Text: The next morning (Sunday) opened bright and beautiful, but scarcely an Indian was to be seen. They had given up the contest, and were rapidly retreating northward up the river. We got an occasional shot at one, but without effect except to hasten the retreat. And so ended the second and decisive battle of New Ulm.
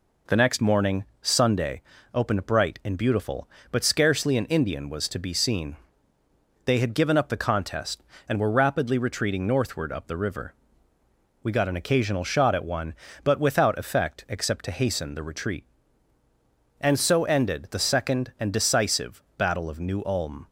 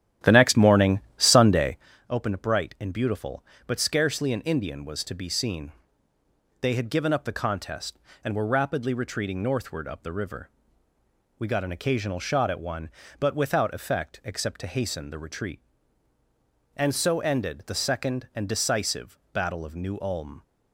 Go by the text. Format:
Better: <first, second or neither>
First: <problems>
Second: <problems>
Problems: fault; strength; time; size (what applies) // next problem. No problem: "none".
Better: first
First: pauses between "decisive" and "battle"; slight; at 19.2 s; 0.16 s long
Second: starts louder than the rest; strong; until 1.9 s; 11.5 dB // pauses between "decisive" and "battle"; slight; at 19.1 s; 0.16 s long